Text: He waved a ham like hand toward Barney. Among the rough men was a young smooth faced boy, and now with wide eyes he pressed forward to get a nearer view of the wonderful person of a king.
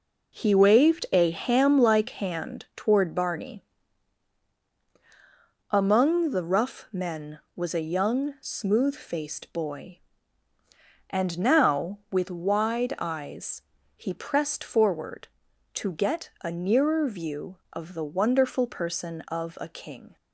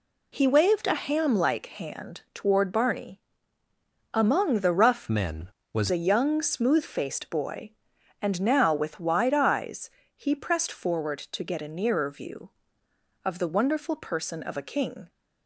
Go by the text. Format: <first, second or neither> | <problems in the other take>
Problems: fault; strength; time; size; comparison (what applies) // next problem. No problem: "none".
first | changes voice from "men" to "was"; from 5.0 to 5.8 s; 0.8 s long // pauses between "eyes" and "he"; slight; at 9.8 s; 0.26 s long; slight in the first